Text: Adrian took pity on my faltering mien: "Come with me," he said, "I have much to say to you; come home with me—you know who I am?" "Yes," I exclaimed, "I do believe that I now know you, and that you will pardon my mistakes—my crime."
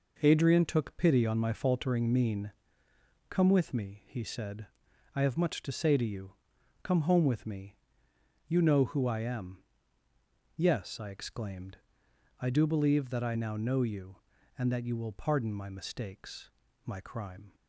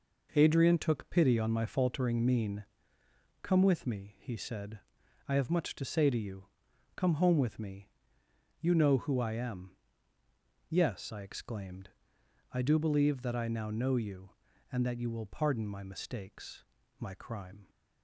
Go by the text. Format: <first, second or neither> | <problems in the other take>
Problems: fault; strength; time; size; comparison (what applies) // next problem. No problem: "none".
neither | none